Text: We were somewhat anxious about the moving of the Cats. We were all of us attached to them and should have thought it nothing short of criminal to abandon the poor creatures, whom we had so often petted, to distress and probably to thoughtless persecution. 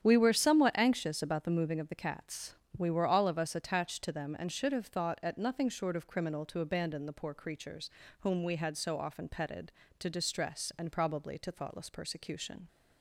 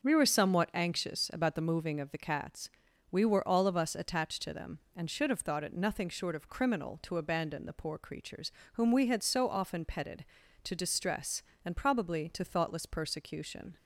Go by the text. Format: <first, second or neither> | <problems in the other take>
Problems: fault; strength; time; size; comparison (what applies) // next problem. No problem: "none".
second | starts louder than the rest; strong; until 1.0 s; 9 dB; also in the second // says "at" for "it"; at 5.2 s